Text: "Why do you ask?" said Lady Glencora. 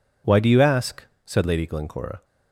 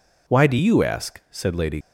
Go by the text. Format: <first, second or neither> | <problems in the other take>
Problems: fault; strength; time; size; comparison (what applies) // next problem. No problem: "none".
first | stops before "Glencora"; at 1.8 s